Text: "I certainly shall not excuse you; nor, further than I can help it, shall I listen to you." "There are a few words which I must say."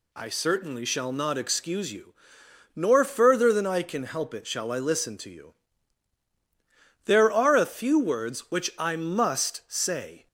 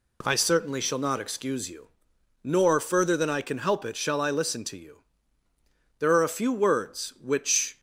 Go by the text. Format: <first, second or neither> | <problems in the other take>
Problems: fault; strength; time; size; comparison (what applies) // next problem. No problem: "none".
first | stops before "I must say"; at 7.7 s